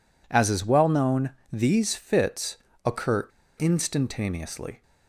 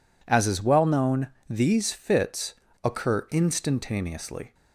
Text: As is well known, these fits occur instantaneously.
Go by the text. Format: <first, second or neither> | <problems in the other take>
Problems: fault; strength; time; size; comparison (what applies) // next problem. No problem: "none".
second | pauses between "fits" and "occur"; slight; at 2.5 s; 0.28 s long; slight in the second // pauses between "occur" and "instantaneously"; slight; at 3.2 s; 0.30 s long